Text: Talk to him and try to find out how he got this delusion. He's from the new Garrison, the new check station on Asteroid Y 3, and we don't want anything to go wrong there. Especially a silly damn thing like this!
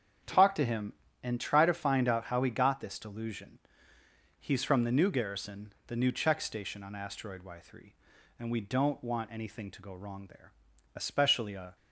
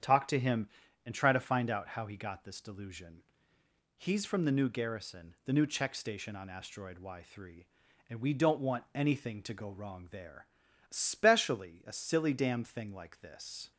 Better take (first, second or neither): second